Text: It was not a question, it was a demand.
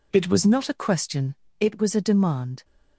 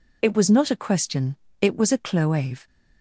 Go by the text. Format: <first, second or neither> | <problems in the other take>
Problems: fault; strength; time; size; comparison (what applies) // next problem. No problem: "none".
first | says "cloave" for "demand"; at 1.9 s